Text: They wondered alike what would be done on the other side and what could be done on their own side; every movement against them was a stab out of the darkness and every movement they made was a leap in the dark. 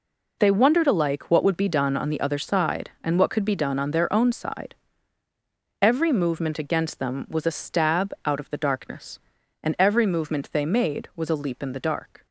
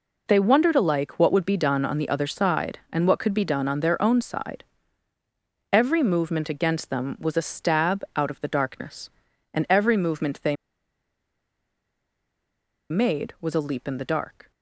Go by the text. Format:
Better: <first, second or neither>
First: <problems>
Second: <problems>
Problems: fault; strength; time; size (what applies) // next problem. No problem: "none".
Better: first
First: none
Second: pauses between "they" and "made"; strong; at 10.5 s; 2.3 s long